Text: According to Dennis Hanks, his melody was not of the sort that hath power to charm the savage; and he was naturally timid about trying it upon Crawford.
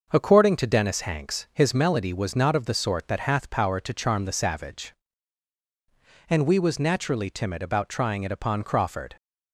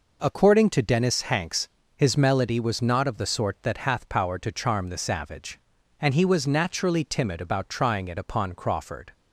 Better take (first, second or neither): second